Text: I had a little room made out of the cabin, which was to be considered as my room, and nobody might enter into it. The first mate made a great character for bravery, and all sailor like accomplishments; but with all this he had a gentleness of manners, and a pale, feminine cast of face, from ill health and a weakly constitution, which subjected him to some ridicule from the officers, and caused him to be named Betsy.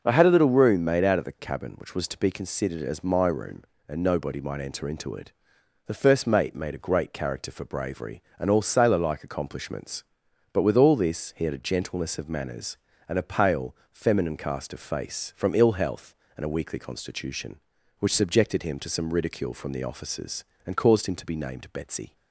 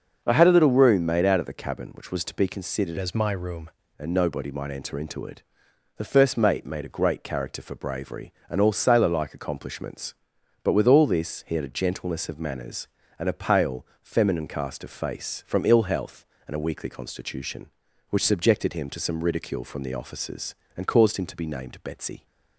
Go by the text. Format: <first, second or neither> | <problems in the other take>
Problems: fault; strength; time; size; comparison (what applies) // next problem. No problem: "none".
first | starts louder than the rest; until 1.2 s; 6 dB // changes voice from "as" to "room"; from 2.9 to 3.7 s; 0.8 s long